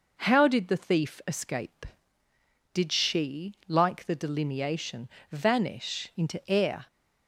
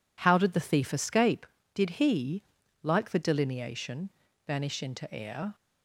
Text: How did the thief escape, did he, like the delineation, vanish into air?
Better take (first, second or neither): second